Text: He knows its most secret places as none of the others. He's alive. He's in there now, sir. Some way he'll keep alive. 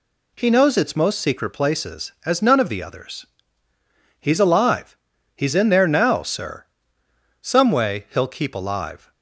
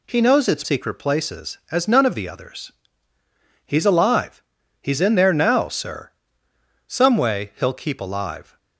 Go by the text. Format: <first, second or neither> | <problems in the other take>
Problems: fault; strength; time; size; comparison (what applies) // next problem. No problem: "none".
first | skips "most"; at 0.6 s